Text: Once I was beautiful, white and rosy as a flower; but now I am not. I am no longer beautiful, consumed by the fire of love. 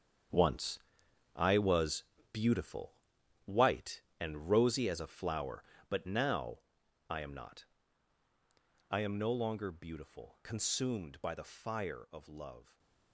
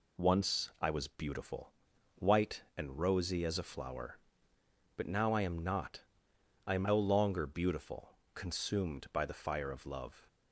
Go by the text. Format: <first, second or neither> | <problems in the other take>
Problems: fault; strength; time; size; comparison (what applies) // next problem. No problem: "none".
second | gets quieter; strong; throughout; 12 dB // pauses between "Once" and "I"; noticeable; at 0.7 s; 0.56 s long // pauses between "was" and "beautiful"; slight; at 2.0 s; 0.26 s long // pauses between "now" and "I"; noticeable; at 6.6 s; 0.48 s long // stays silent after the last word; slight; from 12.6 s on; 0.5 s long